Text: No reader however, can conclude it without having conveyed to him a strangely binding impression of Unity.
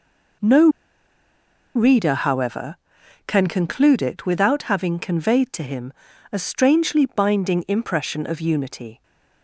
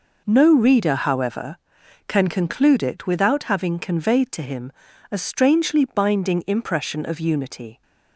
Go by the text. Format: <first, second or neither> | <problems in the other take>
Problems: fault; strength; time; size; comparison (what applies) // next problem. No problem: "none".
second | pauses between "No" and "reader"; at 0.6 s; 1.0 s long // pauses between "him" and "a"; at 5.9 s; 0.38 s long; also in the second